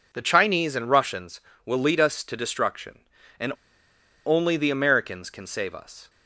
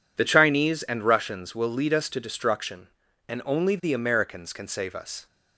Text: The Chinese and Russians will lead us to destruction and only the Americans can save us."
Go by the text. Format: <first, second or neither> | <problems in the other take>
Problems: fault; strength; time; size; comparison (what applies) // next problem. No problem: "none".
second | pauses between "and" and "only"; noticeable; at 3.5 s; 0.74 s long